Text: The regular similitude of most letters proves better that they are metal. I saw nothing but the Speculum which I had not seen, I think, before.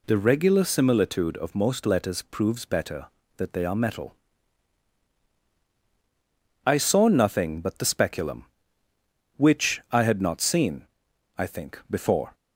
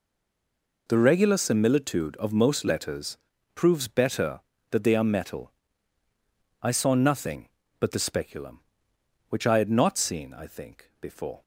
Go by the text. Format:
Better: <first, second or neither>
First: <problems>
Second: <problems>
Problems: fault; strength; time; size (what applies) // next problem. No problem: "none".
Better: first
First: none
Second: stays silent before the first word; slight; until 0.8 s; 0.8 s long // pauses between "letters" and "proves"; at 3.1 s; 0.38 s long